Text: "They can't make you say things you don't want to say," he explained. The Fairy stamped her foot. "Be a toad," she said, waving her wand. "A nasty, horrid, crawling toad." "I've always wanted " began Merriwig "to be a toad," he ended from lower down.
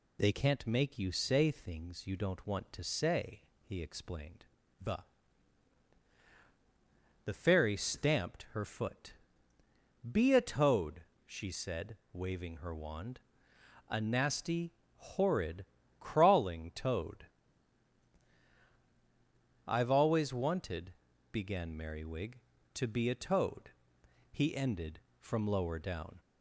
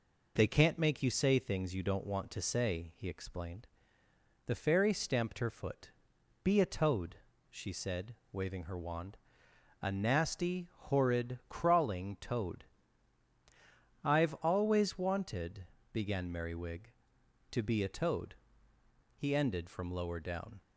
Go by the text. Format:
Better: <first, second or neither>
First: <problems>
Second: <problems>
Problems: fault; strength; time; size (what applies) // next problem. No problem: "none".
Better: second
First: says "The" twice; at 7.2 s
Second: none